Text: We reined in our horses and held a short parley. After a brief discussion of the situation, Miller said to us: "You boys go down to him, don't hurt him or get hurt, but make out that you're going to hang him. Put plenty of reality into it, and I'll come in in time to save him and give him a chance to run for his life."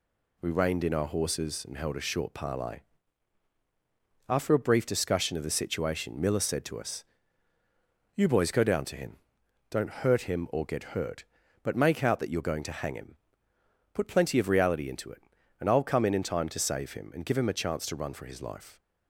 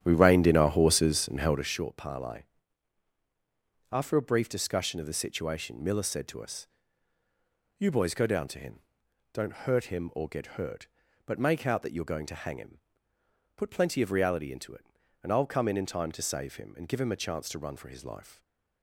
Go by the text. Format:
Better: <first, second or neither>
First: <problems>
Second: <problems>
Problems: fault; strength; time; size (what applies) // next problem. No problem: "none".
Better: first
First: none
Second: starts louder than the rest; strong; until 1.8 s; 10 dB